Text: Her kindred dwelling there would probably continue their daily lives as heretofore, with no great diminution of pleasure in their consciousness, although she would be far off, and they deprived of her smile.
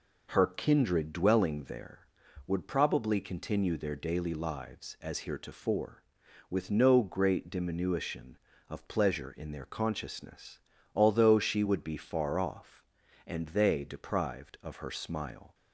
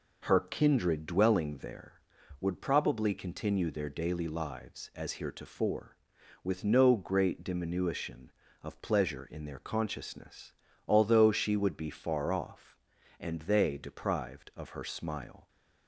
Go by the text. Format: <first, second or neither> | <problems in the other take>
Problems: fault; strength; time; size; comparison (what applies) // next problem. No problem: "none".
neither | none